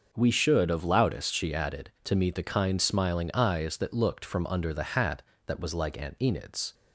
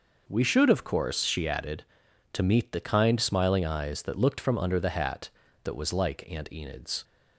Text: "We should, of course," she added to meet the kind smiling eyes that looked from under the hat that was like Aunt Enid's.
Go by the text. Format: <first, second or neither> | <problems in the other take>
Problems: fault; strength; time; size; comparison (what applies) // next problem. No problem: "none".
second | starts louder than the rest; until 1.1 s; 6 dB // says "loudest" for "course"; at 0.8 s